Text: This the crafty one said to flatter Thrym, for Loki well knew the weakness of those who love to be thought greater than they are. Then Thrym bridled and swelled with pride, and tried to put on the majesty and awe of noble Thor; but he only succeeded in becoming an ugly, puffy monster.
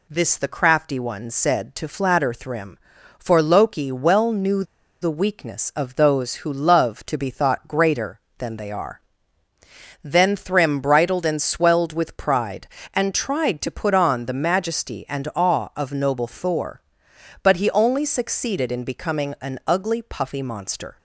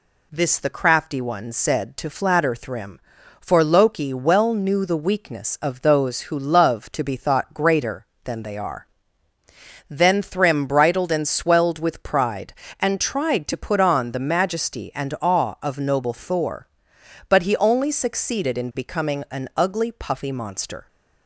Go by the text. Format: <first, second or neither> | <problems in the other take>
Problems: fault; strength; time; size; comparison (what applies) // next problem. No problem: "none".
second | pauses between "knew" and "the"; at 4.6 s; 0.37 s long